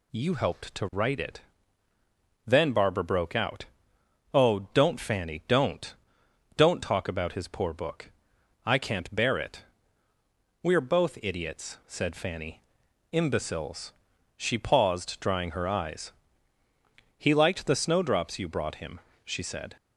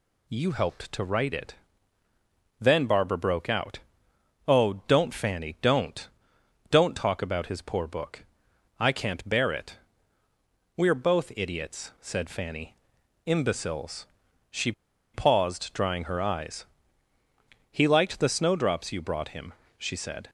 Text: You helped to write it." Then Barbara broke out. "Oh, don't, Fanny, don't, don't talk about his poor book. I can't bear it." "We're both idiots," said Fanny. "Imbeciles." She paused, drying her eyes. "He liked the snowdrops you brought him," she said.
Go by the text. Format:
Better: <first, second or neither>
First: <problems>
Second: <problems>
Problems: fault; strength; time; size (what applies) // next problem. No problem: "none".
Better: first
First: none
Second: pauses between "She" and "paused"; at 14.7 s; 0.42 s long